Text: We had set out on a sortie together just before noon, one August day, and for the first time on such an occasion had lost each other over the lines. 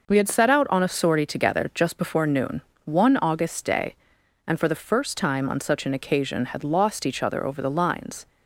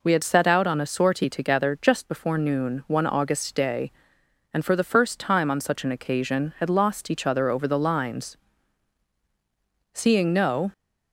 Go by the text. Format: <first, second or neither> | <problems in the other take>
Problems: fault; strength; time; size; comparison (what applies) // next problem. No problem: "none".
first | goes on to say "Seeing no"; noticeable; from 9.9 s on; 0.80 s long